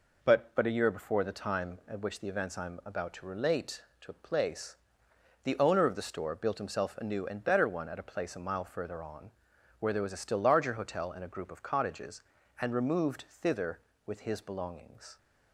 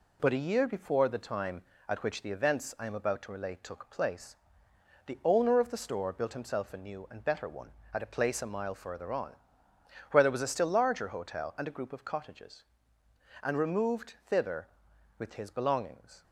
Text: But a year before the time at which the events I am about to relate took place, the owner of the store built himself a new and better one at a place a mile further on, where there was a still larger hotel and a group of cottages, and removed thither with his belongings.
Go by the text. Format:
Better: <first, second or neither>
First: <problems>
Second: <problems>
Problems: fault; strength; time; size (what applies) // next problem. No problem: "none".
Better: second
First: says "But" twice; at 0.5 s // pauses between "relate" and "took"; slight; at 3.8 s; 0.18 s long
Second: none